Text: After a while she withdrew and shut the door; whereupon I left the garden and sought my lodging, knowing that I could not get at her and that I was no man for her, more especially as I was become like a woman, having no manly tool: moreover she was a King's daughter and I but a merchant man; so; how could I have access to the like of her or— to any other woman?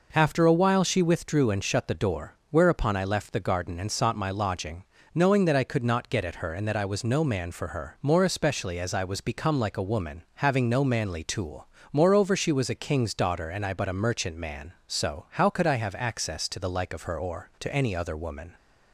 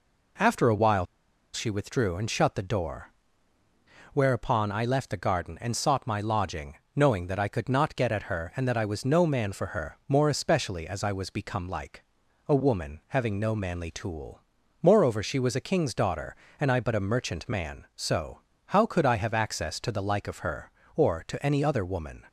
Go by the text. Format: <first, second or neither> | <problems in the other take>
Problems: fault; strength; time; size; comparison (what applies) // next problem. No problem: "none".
first | pauses between "while" and "she"; noticeable; at 1.0 s; 0.48 s long // pauses between "like" and "a"; at 12.0 s; 0.42 s long